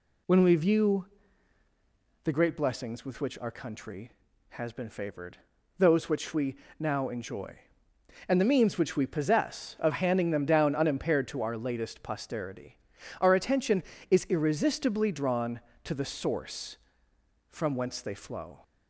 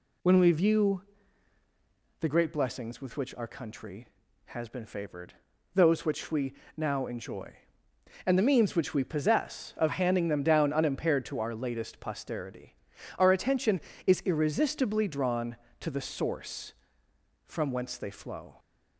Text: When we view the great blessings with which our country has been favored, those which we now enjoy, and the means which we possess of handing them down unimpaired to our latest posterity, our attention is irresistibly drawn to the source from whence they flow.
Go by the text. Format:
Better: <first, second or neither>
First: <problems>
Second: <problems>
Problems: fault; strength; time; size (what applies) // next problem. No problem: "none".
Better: neither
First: pauses between "view" and "the"; at 1.0 s; 1.2 s long // pauses between "we" and "now"; slight; at 6.5 s; 0.24 s long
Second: pauses between "view" and "the"; at 1.0 s; 1.2 s long // pauses between "we" and "now"; slight; at 6.5 s; 0.24 s long